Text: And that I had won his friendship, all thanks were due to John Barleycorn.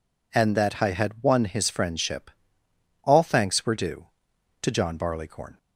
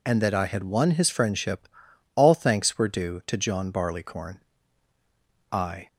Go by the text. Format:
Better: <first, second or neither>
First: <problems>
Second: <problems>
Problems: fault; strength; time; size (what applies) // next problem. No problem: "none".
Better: first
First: none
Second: goes on to say "I"; slight; from 5.5 s on; 0.36 s long